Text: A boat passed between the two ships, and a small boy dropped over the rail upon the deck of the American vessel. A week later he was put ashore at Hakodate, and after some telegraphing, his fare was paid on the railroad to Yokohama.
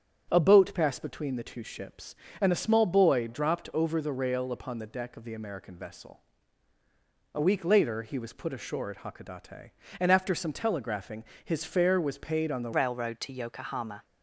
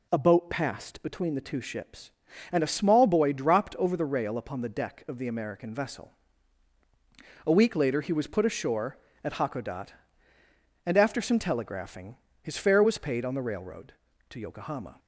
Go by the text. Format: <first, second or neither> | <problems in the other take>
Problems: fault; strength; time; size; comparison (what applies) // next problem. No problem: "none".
second | starts louder than the rest; strong; until 1.3 s; 8 dB // changes voice at "railroad"; from 12.7 s on; 1.3 s long